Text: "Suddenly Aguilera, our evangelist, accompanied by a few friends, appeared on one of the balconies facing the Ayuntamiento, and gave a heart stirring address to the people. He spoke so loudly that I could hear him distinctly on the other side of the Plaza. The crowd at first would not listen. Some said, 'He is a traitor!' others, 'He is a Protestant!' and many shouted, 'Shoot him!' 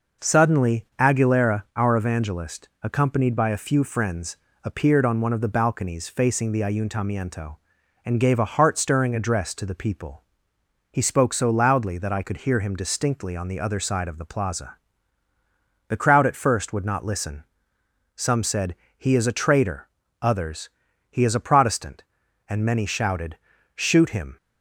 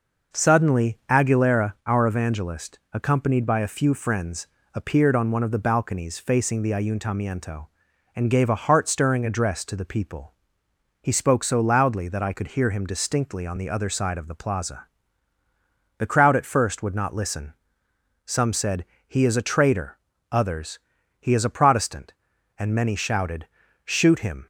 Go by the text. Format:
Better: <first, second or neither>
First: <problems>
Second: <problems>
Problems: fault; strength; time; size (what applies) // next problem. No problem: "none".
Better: neither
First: none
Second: none